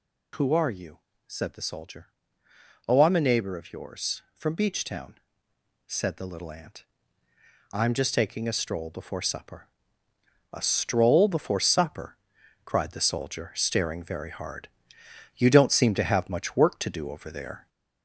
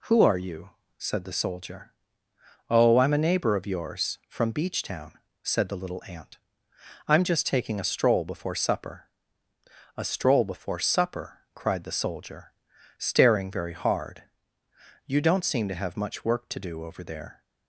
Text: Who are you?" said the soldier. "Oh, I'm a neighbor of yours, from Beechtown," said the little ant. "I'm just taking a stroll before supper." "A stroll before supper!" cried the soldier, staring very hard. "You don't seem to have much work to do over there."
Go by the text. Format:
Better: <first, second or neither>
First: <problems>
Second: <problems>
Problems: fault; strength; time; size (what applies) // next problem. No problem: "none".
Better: second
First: gets louder; slight; throughout; 2.5 dB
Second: none